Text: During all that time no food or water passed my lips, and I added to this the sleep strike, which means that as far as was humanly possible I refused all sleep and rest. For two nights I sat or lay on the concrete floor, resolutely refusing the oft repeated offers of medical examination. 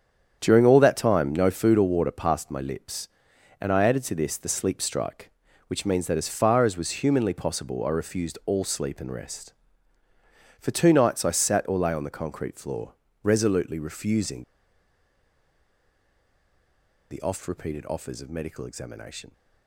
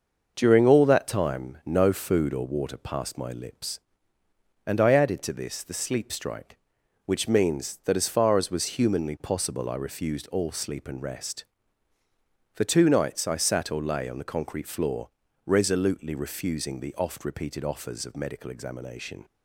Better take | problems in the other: second | starts louder than the rest; strong; until 1.4 s; 8 dB; noticeable in the second // pauses between "refusing" and "the"; strong; at 14.4 s; 2.6 s long

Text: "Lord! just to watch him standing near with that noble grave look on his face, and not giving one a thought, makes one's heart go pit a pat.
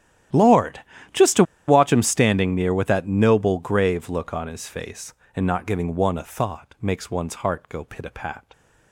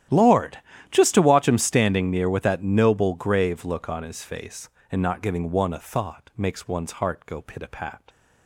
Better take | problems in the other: second | starts louder than the rest; strong; until 1.8 s; 11.5 dB; strong in the second // pauses between "to" and "watch"; slight; at 1.4 s; 0.23 s long

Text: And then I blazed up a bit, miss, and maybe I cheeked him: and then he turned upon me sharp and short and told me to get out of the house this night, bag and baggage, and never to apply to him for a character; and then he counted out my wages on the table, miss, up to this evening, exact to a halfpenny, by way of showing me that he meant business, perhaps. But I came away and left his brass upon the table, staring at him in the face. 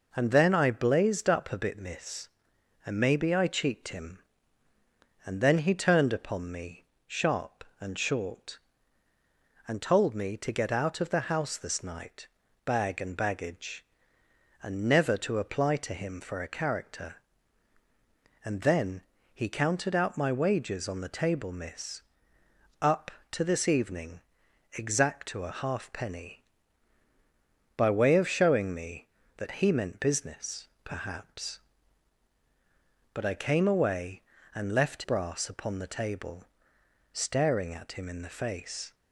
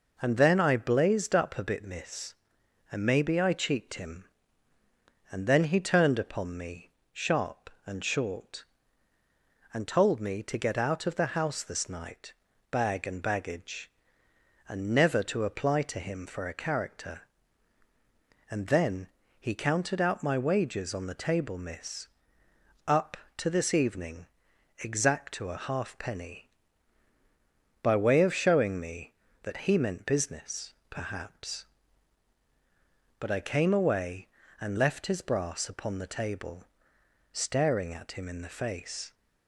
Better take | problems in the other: second | pauses between "me" and "sharp"; slight; at 6.8 s; 0.22 s long; slight in the second // pauses between "then" and "he"; slight; at 19.0 s; 0.30 s long; slight in the second // skips "his"; at 35.0 s

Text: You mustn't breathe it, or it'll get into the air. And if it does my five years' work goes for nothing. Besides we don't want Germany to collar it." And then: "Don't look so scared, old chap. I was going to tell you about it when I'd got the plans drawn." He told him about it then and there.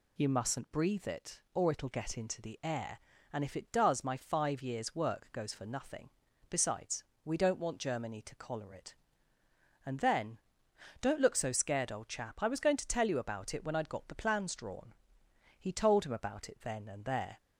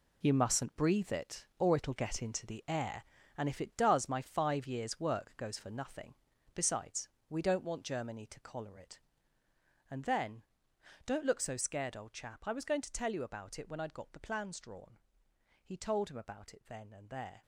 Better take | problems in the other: first | gets quieter; strong; throughout; 10.5 dB // pauses between "Besides" and "we"; slight; at 7.0 s; 0.20 s long; slight in the first

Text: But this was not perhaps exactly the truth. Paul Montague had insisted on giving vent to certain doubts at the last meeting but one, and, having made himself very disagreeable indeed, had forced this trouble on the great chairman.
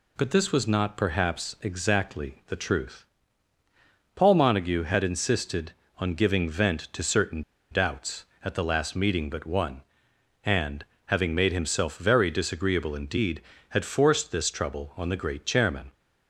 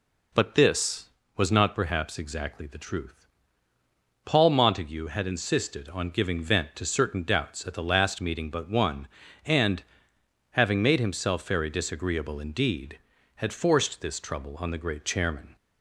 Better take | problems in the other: second | pauses between "certain" and "doubts"; slight; at 7.4 s; 0.29 s long

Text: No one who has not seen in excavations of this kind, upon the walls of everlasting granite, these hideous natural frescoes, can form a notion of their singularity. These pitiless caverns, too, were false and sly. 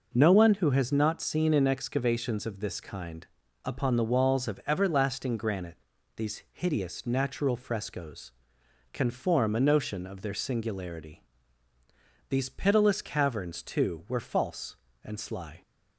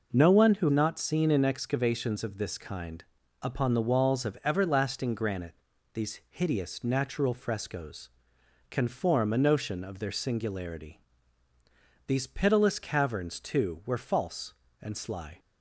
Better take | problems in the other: first | skips "has"; at 0.6 s

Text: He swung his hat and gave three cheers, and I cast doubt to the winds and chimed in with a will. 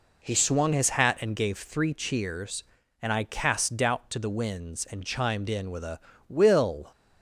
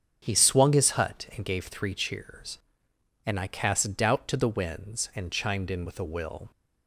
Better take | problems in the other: first | starts louder than the rest; strong; until 1.2 s; 7 dB // says "hut" for "hat"; at 0.9 s

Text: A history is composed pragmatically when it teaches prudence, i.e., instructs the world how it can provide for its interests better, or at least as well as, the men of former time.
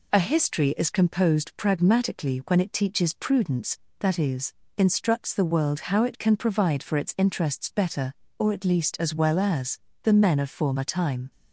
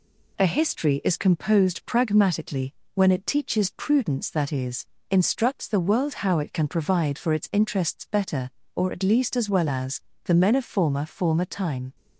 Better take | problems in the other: first | pauses between "pragmatically" and "when"; slight; at 2.7 s; 0.20 s long // says "former" twice; at 11.0 s

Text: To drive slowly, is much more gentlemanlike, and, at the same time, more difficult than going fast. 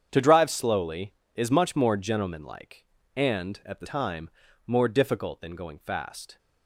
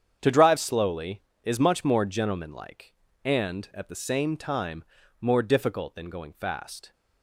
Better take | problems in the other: second | starts louder than the rest; strong; until 1.1 s; 8 dB; strong in the second // skips "same"; at 3.8 s

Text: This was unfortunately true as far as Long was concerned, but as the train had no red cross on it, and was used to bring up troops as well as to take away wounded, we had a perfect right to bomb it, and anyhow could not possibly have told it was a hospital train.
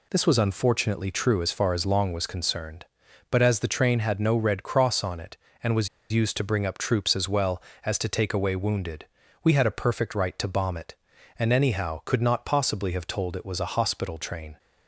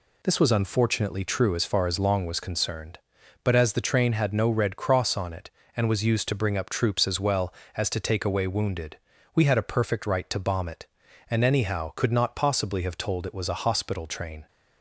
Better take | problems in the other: second | pauses between "was" and "used"; slight; at 5.8 s; 0.24 s long

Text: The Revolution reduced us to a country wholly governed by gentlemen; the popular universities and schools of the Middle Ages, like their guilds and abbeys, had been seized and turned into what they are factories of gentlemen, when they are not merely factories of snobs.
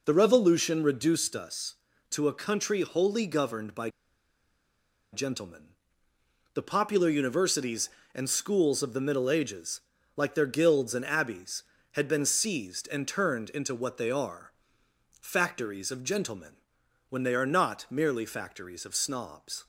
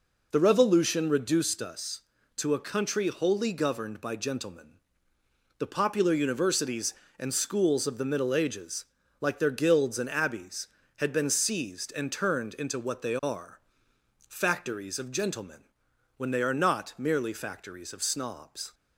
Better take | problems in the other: second | pauses between "by" and "gentlemen"; at 3.8 s; 1.2 s long // pauses between "are" and "factories"; noticeable; at 14.5 s; 0.68 s long; noticeable in the second

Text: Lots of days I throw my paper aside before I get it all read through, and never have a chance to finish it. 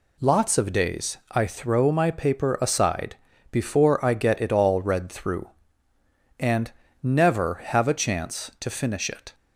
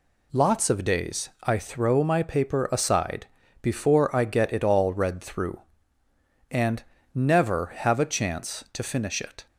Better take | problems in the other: neither | pauses between "aside" and "before"; the same in both // pauses between "and" and "never"; slight; the same in both

